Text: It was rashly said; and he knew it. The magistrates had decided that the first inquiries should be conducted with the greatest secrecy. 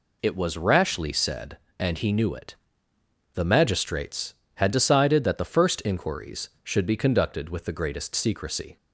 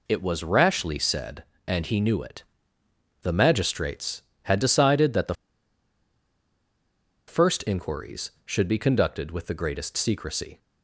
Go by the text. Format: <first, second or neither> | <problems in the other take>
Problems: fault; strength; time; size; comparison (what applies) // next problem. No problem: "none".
first | pauses between "the" and "first"; strong; at 5.3 s; 1.9 s long